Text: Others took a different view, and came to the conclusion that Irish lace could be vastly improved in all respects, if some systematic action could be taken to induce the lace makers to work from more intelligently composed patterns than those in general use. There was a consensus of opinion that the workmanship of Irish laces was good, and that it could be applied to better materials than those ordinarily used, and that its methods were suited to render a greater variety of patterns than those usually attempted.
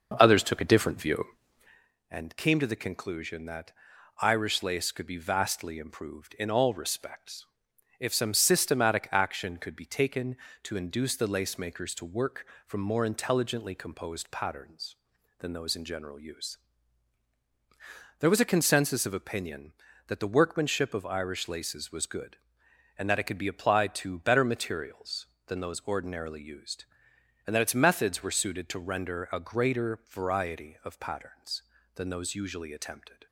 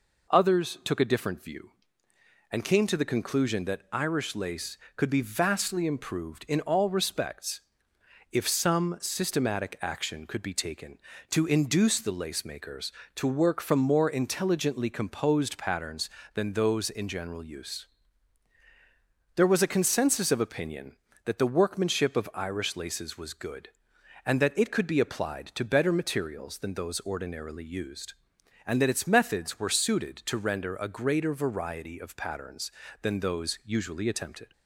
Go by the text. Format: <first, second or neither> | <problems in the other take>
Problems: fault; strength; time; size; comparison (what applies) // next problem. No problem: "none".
second | starts louder than the rest; noticeable; until 1.9 s; 6 dB // pauses between "that" and "Irish"; noticeable; at 3.7 s; 0.48 s long